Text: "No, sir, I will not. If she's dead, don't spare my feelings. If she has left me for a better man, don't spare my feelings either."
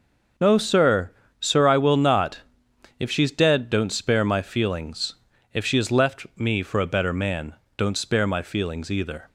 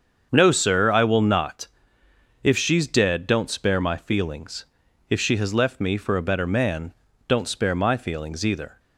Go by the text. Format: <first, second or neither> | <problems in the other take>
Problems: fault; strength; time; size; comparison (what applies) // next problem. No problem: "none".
second | starts louder than the rest; noticeable; until 1.6 s; 6 dB; also in the second // says "sir" twice; at 1.3 s